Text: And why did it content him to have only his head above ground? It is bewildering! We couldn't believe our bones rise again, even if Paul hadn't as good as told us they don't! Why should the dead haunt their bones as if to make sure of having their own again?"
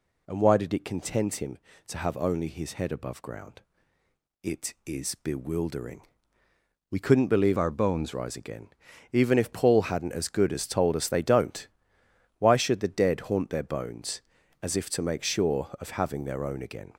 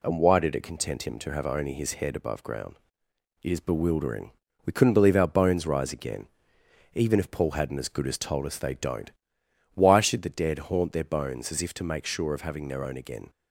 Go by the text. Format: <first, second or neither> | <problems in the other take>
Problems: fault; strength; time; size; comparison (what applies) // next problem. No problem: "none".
second | changes voice from "our" to "bones"; from 7.5 to 8.1 s; 0.6 s long